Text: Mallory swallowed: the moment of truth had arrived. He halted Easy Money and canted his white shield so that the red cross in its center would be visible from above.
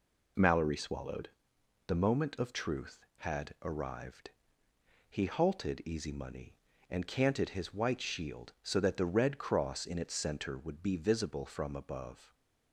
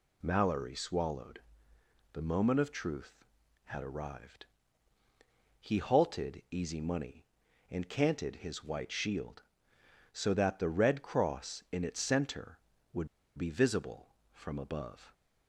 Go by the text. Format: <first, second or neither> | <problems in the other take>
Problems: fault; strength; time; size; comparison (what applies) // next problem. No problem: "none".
first | pauses between "would" and "be"; slight; at 13.0 s; 0.29 s long